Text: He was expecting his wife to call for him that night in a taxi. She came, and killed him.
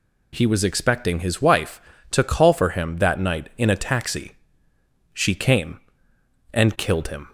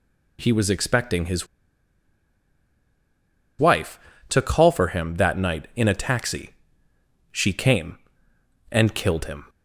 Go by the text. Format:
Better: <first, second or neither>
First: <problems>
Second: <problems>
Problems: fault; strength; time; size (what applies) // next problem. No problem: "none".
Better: first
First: none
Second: pauses between "his" and "wife"; strong; at 1.4 s; 2.1 s long